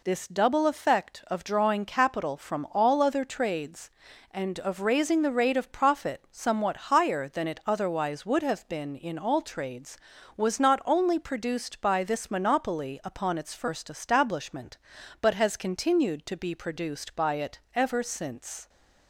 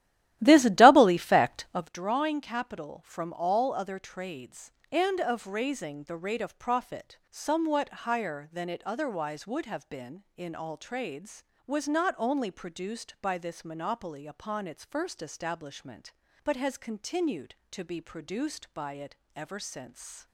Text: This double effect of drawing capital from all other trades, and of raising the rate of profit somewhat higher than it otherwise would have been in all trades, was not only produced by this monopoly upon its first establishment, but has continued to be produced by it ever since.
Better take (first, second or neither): first